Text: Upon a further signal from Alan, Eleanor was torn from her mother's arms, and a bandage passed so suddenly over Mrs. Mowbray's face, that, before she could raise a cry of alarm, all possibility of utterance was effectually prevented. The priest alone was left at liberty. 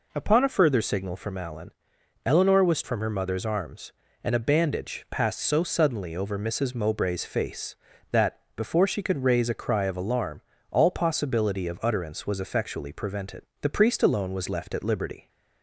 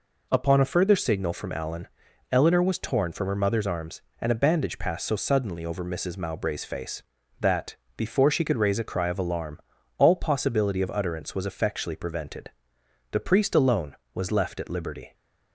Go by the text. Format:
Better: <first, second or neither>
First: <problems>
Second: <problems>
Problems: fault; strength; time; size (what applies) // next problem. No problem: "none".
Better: second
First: skips "torn"; at 2.8 s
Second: none